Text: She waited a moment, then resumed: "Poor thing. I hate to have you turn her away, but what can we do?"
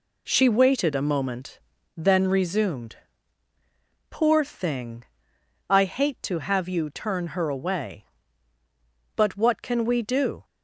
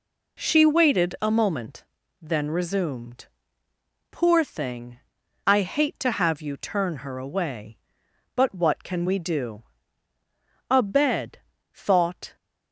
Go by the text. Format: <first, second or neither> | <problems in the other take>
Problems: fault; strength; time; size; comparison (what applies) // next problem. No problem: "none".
first | goes on to say "A bed thought"; from 10.6 s on; 1.6 s long